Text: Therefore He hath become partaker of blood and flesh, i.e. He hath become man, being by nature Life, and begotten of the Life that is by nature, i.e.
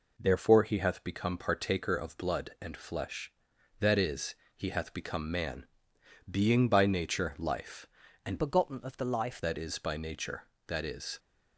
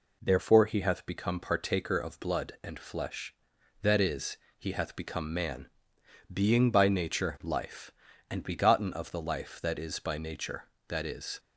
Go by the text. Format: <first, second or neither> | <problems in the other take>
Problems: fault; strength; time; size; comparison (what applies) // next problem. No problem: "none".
second | changes voice from "begotten" to "Life"; from 8.3 to 9.4 s; 1.1 s long